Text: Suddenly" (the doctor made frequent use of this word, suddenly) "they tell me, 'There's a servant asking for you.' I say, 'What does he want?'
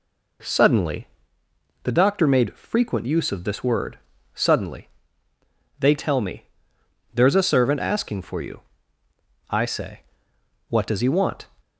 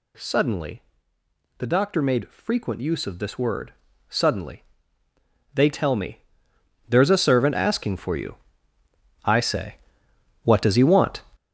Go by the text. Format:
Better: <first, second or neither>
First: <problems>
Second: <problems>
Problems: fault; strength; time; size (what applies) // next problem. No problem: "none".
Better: first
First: none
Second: gets louder; strong; throughout; 10.5 dB